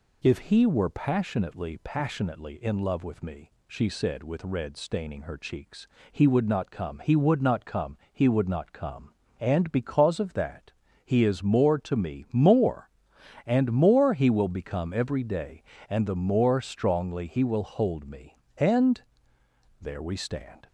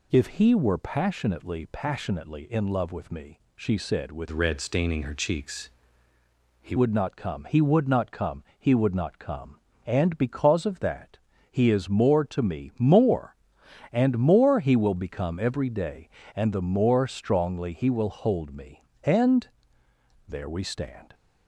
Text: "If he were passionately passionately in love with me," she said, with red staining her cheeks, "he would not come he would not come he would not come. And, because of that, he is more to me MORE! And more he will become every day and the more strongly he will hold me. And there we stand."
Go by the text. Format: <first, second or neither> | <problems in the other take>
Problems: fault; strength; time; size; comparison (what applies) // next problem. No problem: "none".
first | changes voice from "red" to "he"; from 4.3 to 6.7 s; 2.4 s long // pauses between "And" and "there"; noticeable; at 19.4 s; 0.80 s long; noticeable in the first